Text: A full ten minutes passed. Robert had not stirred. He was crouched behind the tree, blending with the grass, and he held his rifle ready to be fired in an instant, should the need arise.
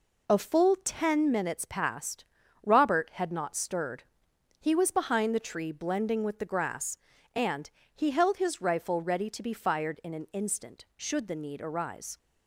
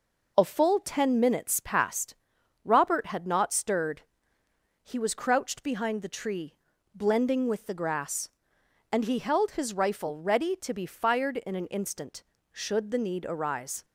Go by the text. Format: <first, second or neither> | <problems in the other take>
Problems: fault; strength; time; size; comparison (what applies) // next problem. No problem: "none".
second | skips "crouched"; at 4.8 s // pauses between "and" and "he"; slight; at 7.6 s; 0.24 s long